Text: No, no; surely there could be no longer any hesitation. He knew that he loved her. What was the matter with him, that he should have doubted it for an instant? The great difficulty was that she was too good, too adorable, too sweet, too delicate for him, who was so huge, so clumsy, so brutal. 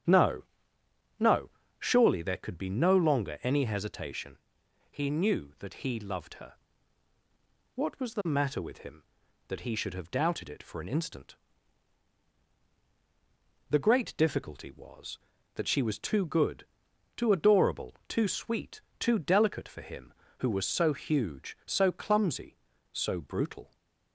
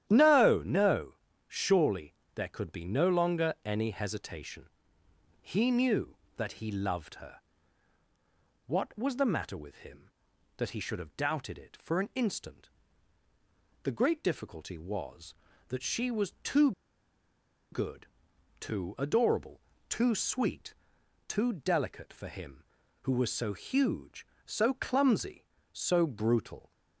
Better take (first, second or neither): first